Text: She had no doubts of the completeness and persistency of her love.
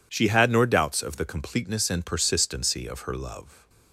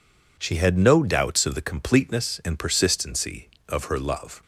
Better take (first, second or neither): second